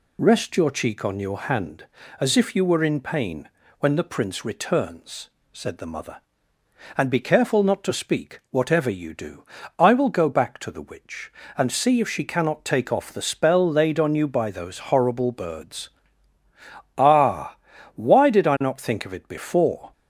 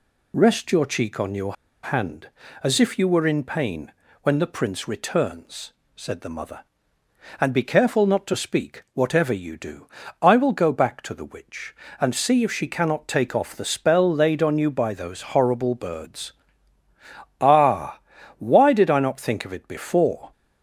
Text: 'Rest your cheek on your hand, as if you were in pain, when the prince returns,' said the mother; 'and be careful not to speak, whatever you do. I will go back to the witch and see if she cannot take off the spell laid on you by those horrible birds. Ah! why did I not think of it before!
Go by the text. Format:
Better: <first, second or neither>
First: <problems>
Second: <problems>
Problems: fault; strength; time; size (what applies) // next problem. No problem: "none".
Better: first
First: none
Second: pauses between "your" and "hand"; slight; at 1.5 s; 0.28 s long